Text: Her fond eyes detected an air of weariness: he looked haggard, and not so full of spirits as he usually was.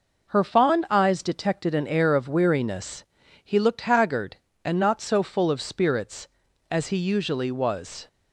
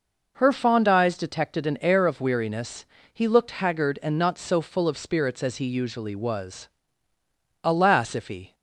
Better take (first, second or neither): first